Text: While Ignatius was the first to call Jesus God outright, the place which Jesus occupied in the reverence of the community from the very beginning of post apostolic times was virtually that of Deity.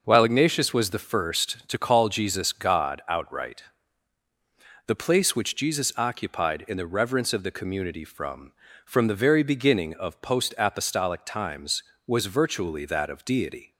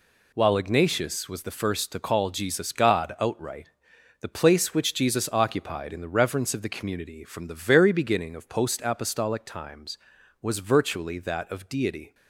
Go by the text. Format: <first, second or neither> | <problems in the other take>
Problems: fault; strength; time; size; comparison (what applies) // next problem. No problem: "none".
second | says "from" twice; at 8.8 s